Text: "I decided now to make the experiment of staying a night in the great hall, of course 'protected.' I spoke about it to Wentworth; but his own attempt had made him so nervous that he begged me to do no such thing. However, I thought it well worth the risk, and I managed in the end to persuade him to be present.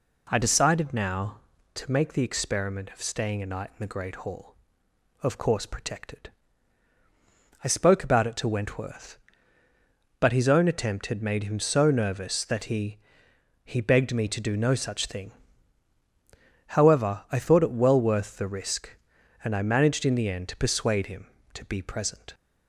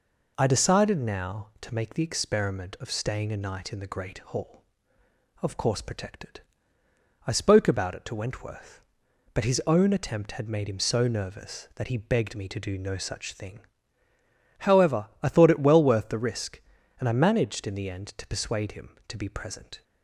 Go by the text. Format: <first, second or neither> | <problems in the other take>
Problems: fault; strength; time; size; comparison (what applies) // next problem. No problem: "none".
second | says "he" twice; at 13.6 s